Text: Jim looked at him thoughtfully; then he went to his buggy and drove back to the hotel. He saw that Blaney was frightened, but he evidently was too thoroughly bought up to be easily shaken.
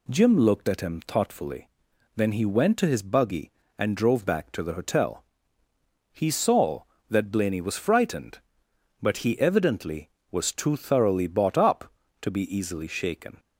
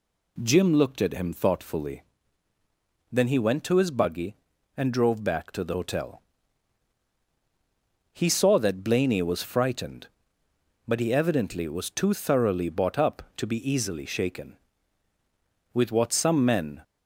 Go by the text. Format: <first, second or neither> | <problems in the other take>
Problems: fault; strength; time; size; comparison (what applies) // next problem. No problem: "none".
first | goes on to say "With what some men"; noticeable; from 15.7 s on; 1.1 s long